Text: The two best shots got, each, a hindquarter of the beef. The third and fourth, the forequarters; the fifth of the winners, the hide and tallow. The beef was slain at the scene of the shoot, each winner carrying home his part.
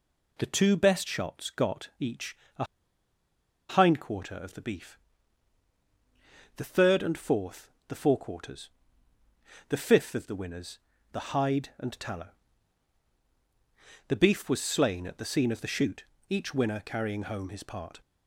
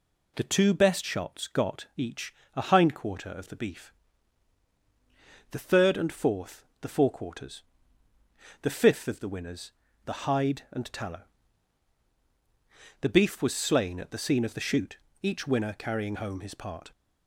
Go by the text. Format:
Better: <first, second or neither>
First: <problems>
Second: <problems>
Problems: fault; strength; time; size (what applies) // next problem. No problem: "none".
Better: second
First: pauses between "a" and "hindquarter"; at 2.6 s; 1.0 s long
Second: none